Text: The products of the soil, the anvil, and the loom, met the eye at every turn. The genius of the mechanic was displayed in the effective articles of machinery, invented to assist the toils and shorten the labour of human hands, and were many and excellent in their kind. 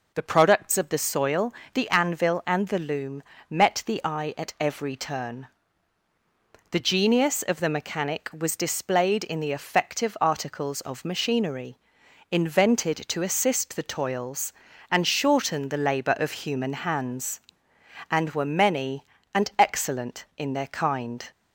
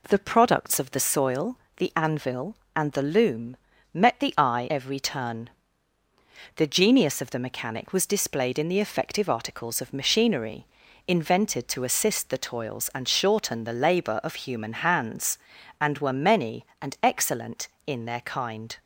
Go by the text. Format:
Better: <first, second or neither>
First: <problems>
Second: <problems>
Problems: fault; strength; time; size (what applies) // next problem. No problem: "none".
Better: first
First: none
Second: skips "at"; at 4.6 s